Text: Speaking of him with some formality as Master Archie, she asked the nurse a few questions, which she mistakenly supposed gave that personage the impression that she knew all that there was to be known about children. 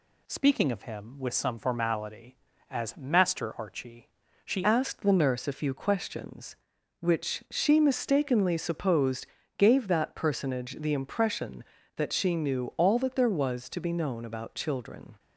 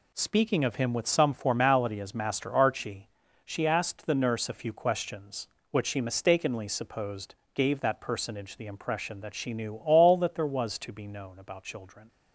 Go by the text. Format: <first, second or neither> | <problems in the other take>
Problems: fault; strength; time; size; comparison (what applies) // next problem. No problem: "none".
second | changes voice at "asked"; from 4.6 s on; 10.5 s long // pauses between "supposed" and "gave"; slight; at 9.2 s; 0.32 s long; slight in the second